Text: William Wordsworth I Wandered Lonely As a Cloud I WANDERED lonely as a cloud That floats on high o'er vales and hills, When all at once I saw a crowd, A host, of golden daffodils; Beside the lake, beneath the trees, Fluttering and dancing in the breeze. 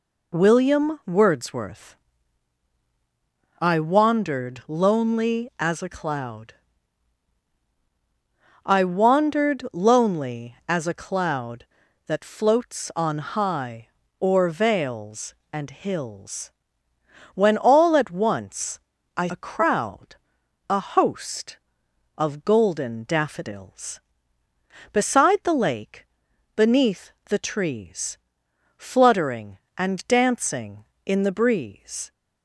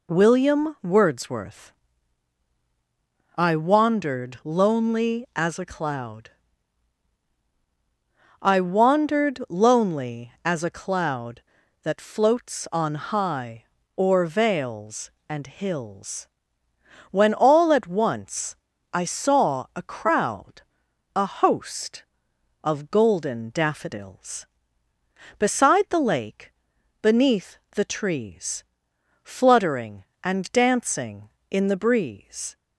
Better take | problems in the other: second | pauses between "Wordsworth" and "I"; strong; at 1.9 s; 1.6 s long; strong in the second // pauses between "Cloud" and "I"; strong; at 6.5 s; 2.1 s long; strong in the second // pauses between "high" and "o'er"; slight; at 13.8 s; 0.30 s long; slight in the second // pauses between "once" and "I"; slight; at 18.7 s; 0.36 s long; slight in the second // skips "saw"; at 19.2 s // pauses between "beneath" and "the"; slight; at 27.1 s; 0.18 s long; slight in the second

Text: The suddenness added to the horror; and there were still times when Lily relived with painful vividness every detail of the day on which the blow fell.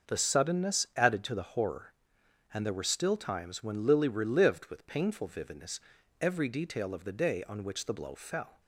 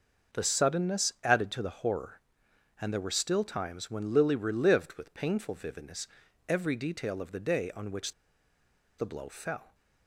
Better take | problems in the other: first | starts louder than the rest; until 1.4 s; 6 dB; also in the first // pauses between "vividness" and "every"; at 6.0 s; 0.40 s long; also in the first // pauses between "which" and "the"; noticeable; at 8.1 s; 0.85 s long

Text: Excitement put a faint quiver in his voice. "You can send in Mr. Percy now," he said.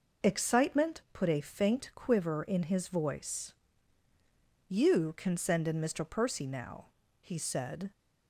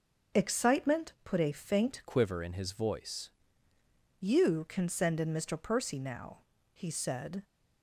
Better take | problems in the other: first | changes voice from "quiver" to "voice"; from 2.0 to 3.2 s; 1.2 s long

